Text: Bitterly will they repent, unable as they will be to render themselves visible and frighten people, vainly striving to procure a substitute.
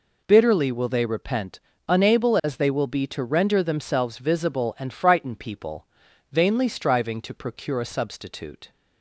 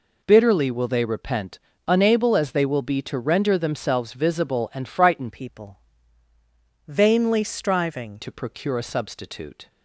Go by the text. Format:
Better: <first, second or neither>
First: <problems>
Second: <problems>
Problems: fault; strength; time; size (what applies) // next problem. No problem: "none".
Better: first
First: none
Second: changes voice from "people" to "striving"; from 5.2 to 8.2 s; 3.0 s long